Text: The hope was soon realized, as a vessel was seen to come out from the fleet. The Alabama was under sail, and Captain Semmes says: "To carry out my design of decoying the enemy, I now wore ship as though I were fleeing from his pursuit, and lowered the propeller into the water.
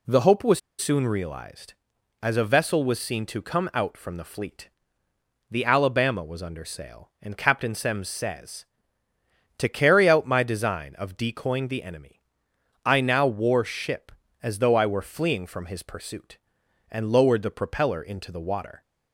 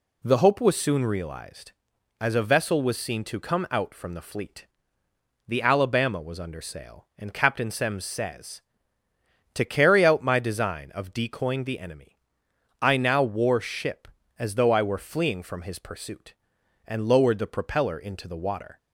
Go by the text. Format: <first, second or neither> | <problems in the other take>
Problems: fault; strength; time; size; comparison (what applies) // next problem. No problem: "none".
second | pauses between "was" and "soon"; slight; at 0.5 s; 0.21 s long